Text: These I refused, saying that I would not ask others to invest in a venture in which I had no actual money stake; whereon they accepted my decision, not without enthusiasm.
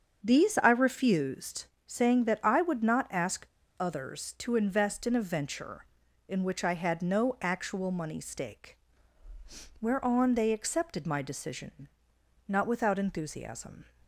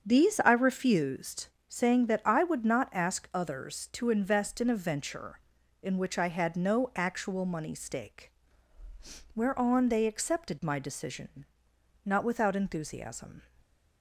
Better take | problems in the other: second | starts louder than the rest; strong; until 1.2 s; 7 dB; strong in the second // pauses between "ask" and "others"; slight; at 3.4 s; 0.31 s long

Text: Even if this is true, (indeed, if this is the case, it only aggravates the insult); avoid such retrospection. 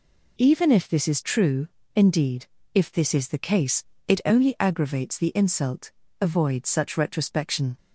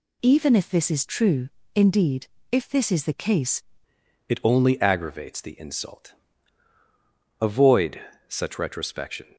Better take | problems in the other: first | changes voice at "it"; from 4.2 s on; 5.1 s long // pauses between "avoid" and "such"; slight; at 8.0 s; 0.26 s long

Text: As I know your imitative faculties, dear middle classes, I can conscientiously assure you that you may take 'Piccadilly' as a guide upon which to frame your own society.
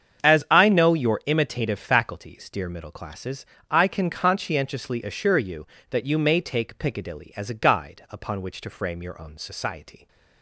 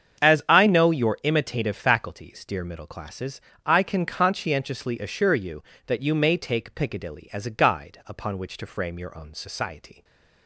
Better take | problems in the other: neither | starts louder than the rest; strong; the same in both

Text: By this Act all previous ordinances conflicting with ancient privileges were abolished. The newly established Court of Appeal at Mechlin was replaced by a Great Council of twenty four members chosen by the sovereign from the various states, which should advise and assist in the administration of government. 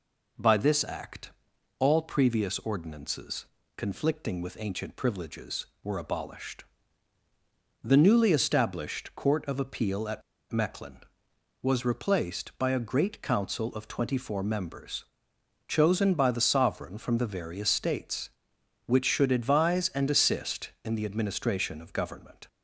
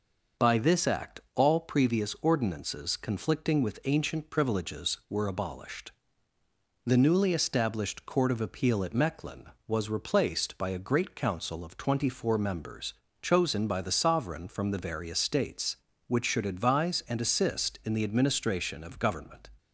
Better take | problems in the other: second | pauses between "Act" and "all"; noticeable; at 1.3 s; 0.46 s long // pauses between "ordinances" and "conflicting"; slight; at 3.4 s; 0.32 s long // pauses between "at" and "Mechlin"; slight; at 10.2 s; 0.29 s long // pauses between "members" and "chosen"; noticeable; at 15.0 s; 0.62 s long; slight in the second

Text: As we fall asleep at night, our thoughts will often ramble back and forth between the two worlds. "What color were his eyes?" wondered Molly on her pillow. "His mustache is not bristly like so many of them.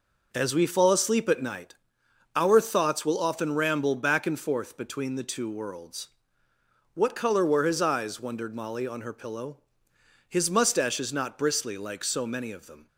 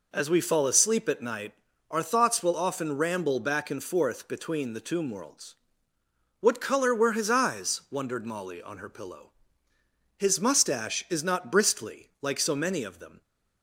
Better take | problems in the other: first | says "tomb" for "two"; at 4.8 s

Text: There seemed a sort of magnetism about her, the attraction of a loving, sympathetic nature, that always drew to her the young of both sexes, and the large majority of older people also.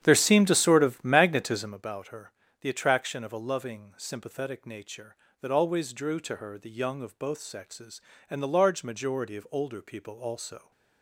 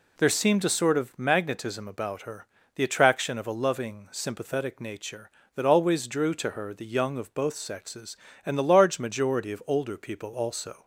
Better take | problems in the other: second | starts louder than the rest; strong; until 1.8 s; 9.5 dB

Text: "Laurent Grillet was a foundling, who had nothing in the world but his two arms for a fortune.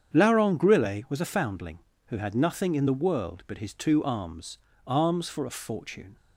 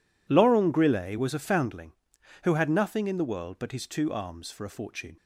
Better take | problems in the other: second | starts louder than the rest; strong; until 1.1 s; 8 dB // says "arms" twice; at 4.8 s

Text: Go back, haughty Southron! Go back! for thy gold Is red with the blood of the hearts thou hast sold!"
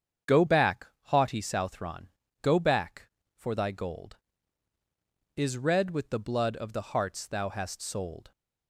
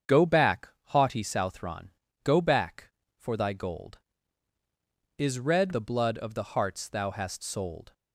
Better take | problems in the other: first | starts louder than the rest; strong; until 1.2 s; 7.5 dB; strong in the first // skips "with"; at 5.7 s

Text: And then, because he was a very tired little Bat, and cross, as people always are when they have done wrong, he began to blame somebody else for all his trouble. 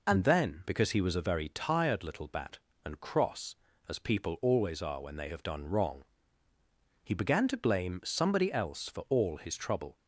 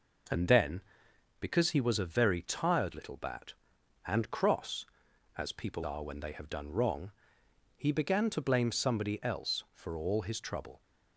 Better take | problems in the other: first | skips "always"; at 5.8 s

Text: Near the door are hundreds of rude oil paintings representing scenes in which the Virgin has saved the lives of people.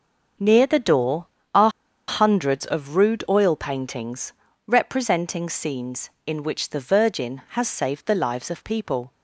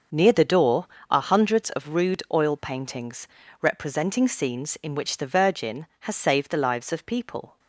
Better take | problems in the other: second | starts louder than the rest; until 1.6 s; 6.5 dB; also in the second // pauses between "are" and "hundreds"; at 1.7 s; 0.37 s long // pauses between "paintings" and "representing"; slight; at 4.3 s; 0.34 s long; slight in the second

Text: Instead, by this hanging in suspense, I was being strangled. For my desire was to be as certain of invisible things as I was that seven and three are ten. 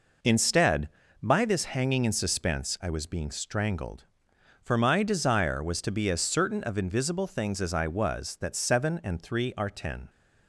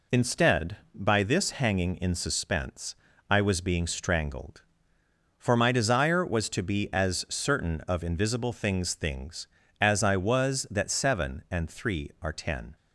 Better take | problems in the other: first | says "things" twice; at 8.9 s

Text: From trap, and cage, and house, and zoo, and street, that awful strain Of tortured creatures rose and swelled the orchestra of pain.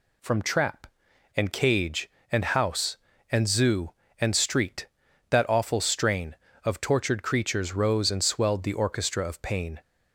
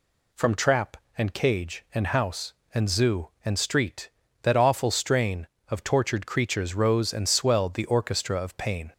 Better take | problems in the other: neither | none

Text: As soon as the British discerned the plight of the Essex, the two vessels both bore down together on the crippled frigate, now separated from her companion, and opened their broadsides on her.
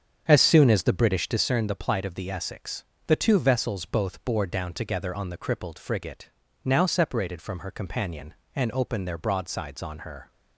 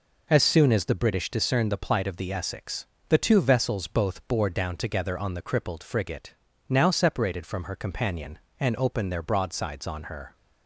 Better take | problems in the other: second | starts louder than the rest; strong; until 1.5 s; 7.5 dB

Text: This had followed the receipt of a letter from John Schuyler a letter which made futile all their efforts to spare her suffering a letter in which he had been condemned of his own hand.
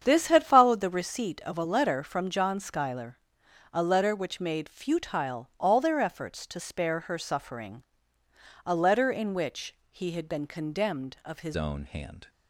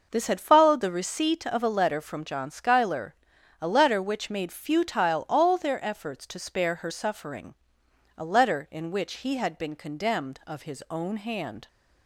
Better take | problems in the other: second | starts louder than the rest; strong; until 1.0 s; 8 dB // pauses between "Schuyler" and "a"; noticeable; at 3.1 s; 0.54 s long; noticeable in the second // pauses between "suffering" and "a"; noticeable; at 7.8 s; 0.82 s long; noticeable in the second // pauses between "which" and "he"; slight; at 9.7 s; 0.16 s long // changes voice at "own"; from 11.5 s on; 0.7 s long

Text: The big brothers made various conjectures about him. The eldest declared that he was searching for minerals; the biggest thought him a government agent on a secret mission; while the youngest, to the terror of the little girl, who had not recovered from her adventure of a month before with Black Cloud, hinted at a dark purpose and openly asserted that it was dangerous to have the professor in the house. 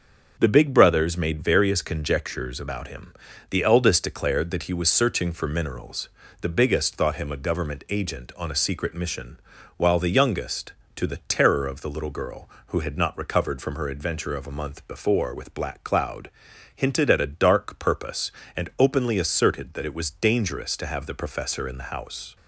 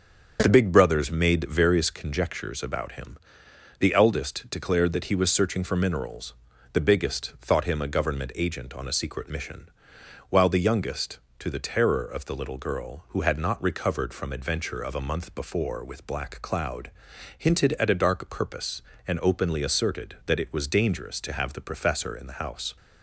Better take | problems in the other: first | starts louder than the rest; until 1.4 s; 7 dB; also in the first // skips "her"; at 14.3 s

